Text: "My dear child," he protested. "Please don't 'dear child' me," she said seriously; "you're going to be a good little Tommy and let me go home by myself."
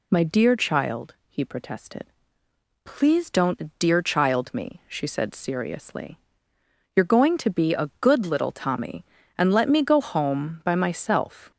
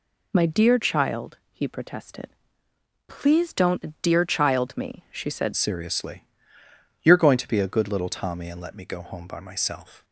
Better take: first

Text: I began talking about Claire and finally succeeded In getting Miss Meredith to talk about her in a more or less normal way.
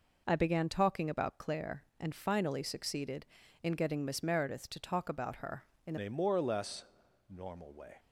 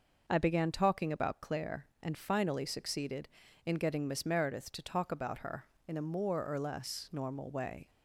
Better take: second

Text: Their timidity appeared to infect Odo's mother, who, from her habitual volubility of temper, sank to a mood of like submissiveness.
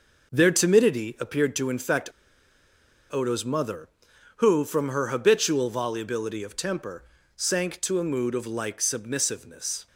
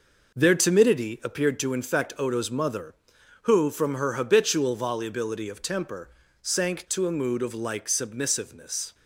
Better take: second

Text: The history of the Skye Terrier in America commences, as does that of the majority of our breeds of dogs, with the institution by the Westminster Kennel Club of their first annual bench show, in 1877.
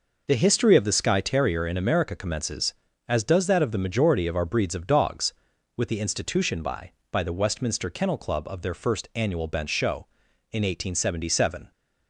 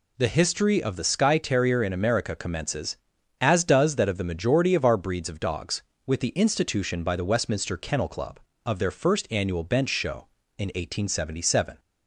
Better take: second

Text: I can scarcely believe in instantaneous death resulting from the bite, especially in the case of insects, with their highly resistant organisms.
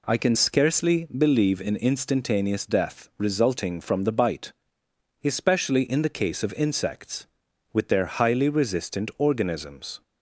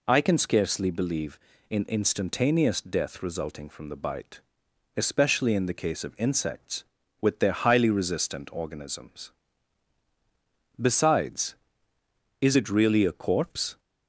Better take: first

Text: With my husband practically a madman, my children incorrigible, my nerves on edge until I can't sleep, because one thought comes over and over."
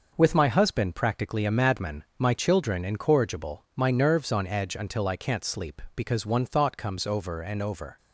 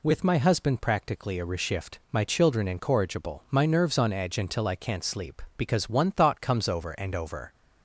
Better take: first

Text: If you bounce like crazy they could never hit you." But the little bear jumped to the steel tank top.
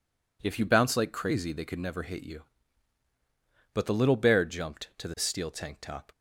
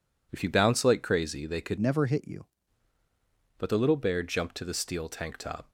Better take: first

